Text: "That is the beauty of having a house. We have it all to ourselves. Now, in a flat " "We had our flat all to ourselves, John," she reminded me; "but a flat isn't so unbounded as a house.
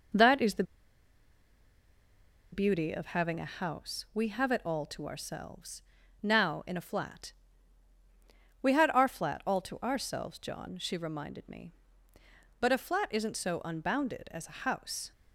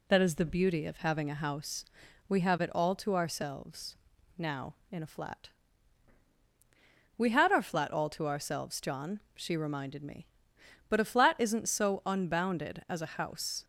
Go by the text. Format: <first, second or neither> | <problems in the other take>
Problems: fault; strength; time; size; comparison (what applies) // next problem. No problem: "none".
second | pauses between "the" and "beauty"; strong; at 0.6 s; 1.8 s long